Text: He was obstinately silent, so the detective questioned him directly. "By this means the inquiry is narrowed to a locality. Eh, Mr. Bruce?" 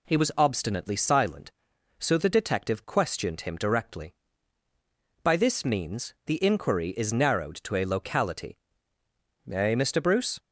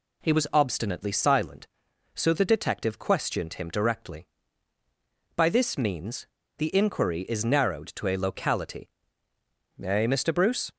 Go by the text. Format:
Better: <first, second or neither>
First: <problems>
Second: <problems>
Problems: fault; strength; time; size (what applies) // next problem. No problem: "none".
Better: first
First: none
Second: pauses between "means" and "the"; slight; at 6.2 s; 0.28 s long